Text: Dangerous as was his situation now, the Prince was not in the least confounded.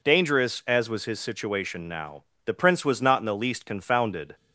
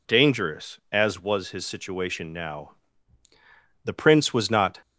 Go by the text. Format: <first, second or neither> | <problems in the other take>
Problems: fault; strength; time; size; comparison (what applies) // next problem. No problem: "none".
first | stops before "in the least confounded"; at 4.8 s